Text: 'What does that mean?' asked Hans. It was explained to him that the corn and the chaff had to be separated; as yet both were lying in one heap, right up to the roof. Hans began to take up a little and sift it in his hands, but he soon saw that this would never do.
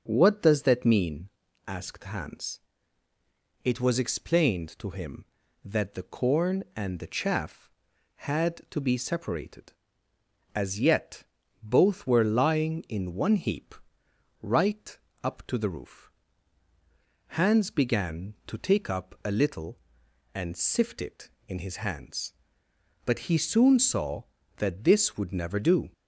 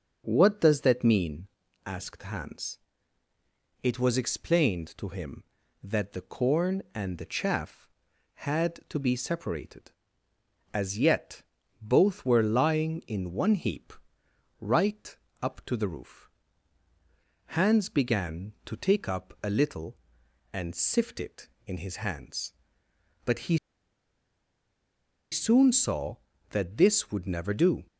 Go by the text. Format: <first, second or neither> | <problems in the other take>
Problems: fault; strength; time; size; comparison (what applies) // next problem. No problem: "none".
first | starts louder than the rest; until 1.2 s; 7 dB; also in the first // pauses between "yet" and "both"; slight; at 11.4 s; 0.36 s long; slight in the first // pauses between "right" and "up"; slight; at 15.1 s; 0.28 s long; slight in the first // pauses between "he" and "soon"; strong; at 23.5 s; 1.7 s long